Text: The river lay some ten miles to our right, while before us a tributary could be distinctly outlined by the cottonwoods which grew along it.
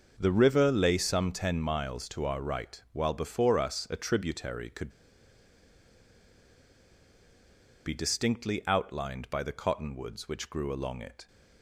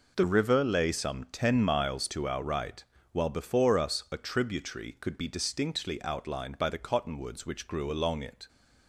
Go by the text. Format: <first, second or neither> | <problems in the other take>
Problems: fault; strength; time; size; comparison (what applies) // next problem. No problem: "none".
second | starts louder than the rest; until 1.1 s; 6 dB // pauses between "could" and "be"; strong; at 4.8 s; 2.9 s long